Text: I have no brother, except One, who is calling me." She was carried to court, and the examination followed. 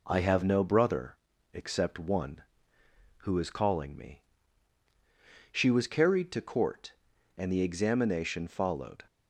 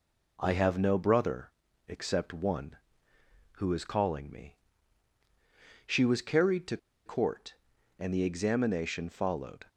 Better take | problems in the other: first | pauses between "to" and "court"; slight; at 6.7 s; 0.28 s long

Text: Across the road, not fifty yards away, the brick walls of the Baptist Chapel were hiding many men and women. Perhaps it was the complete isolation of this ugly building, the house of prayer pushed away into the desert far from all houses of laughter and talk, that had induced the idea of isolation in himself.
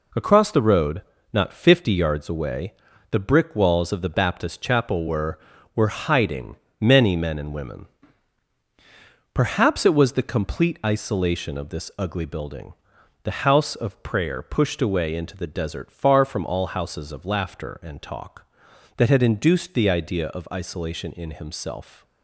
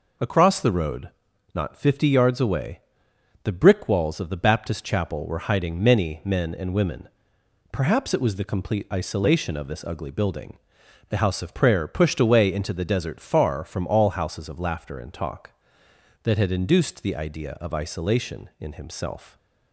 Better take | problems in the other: second | says "were" twice; at 5.7 s // pauses between "hiding" and "many"; slight; at 6.5 s; 0.24 s long

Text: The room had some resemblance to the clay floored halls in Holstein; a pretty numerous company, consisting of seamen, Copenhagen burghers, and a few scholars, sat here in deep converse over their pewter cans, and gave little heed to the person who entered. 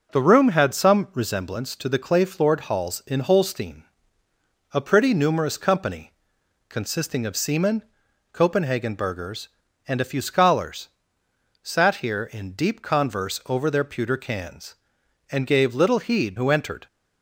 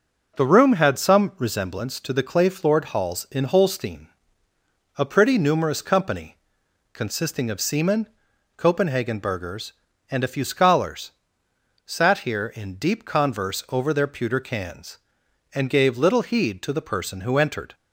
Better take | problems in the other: second | skips "to the person"; at 16.3 s

